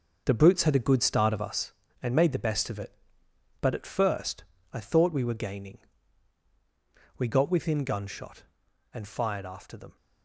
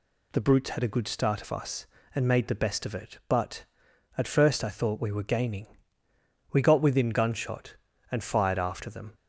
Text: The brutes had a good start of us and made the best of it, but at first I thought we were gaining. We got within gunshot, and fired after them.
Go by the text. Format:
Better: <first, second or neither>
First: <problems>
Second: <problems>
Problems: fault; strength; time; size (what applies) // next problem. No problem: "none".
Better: second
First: gets quieter; strong; throughout; 8.5 dB // pauses between "first" and "I"; slight; at 4.4 s; 0.28 s long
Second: none